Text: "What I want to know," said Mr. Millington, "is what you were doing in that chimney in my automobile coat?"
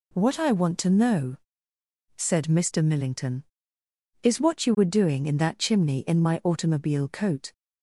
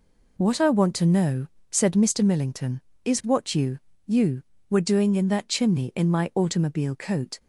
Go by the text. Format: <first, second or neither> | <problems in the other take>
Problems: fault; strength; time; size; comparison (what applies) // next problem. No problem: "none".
first | says "you" twice; at 4.0 s